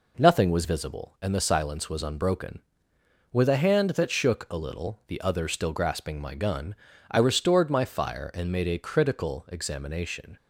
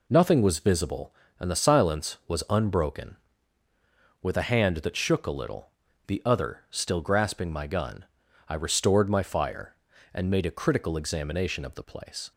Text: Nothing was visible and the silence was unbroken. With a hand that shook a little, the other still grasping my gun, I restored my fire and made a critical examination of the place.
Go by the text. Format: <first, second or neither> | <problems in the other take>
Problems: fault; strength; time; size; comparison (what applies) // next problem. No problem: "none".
second | stops before "of the place"; at 10.3 s